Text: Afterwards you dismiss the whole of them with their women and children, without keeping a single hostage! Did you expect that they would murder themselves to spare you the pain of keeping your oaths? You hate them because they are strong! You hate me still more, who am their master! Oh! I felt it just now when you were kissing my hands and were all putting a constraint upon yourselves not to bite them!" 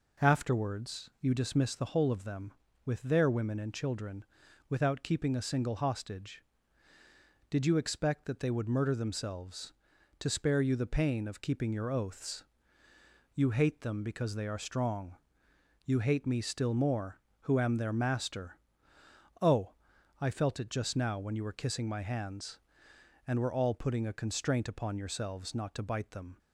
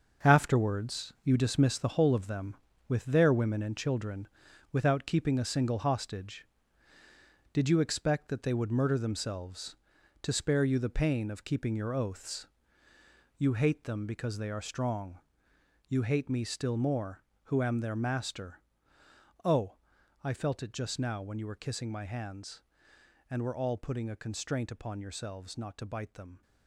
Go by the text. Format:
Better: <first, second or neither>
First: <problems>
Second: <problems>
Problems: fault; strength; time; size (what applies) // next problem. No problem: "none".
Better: first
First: none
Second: gets quieter; strong; throughout; 9 dB